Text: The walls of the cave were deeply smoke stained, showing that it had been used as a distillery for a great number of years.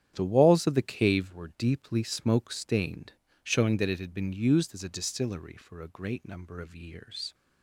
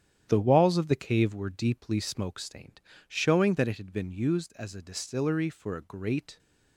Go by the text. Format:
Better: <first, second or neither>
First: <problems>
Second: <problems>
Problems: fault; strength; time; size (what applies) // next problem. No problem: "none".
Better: first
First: starts louder than the rest; strong; until 1.1 s; 9.5 dB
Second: starts louder than the rest; strong; until 1.2 s; 9.5 dB // stops before "number of years"; at 6.3 s